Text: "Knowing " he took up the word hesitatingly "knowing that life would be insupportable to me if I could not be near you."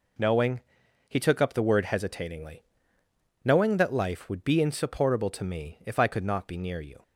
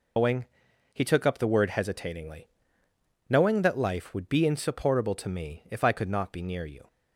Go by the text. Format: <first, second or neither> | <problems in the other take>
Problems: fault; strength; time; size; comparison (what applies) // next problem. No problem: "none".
first | loses the start of "Knowing"; at 0.1 s; 130 ms // pauses between "hesitatingly" and "knowing"; noticeable; at 2.4 s; 0.82 s long; noticeable in the first